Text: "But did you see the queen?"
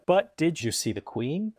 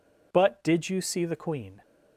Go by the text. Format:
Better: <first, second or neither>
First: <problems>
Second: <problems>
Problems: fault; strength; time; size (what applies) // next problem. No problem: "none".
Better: second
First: changes voice at "you"; from 0.6 s on; 0.9 s long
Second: none